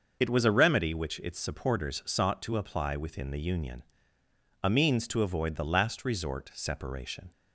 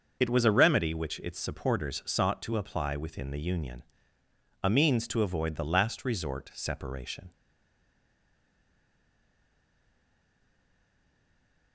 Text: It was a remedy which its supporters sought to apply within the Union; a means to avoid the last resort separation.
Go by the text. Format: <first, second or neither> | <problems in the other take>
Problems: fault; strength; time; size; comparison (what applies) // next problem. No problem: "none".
first | starts louder than the rest; until 1.2 s; 6 dB; also in the first // stays silent after the last word; strong; from 7.3 s on; 4.4 s long